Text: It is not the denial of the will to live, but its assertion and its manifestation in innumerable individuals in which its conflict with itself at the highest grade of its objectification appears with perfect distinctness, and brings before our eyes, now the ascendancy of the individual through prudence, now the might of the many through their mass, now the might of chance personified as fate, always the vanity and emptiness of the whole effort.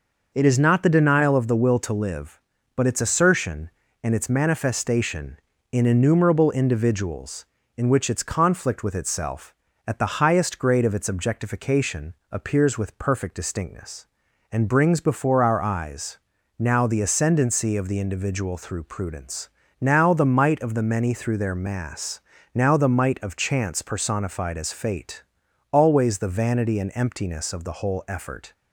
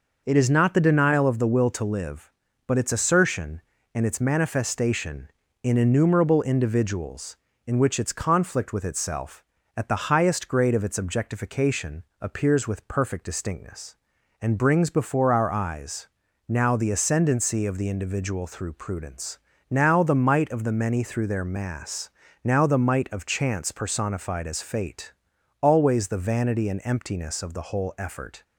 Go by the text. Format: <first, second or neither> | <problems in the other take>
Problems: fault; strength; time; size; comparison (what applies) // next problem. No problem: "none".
neither | pauses between "objectification" and "appears"; slight; the same in both